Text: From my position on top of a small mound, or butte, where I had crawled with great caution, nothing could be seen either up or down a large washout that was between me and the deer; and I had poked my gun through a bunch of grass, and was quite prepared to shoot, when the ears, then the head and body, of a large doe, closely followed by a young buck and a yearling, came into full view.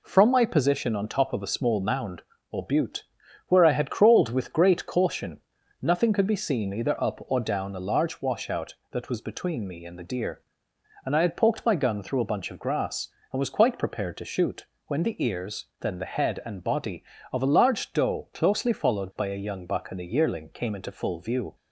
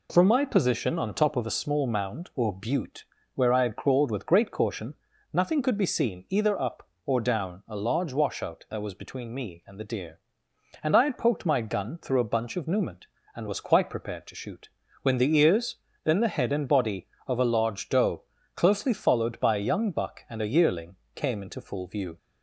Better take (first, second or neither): first